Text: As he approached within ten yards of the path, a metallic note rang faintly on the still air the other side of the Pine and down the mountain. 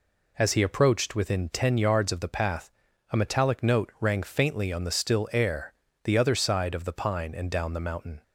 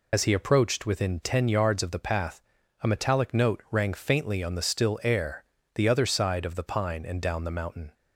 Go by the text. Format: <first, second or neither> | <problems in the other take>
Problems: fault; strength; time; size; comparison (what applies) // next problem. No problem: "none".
first | loses the start of "As"; at 0.1 s; 60 ms // pauses between "air" and "the"; slight; at 5.4 s; 0.30 s long; slight in the first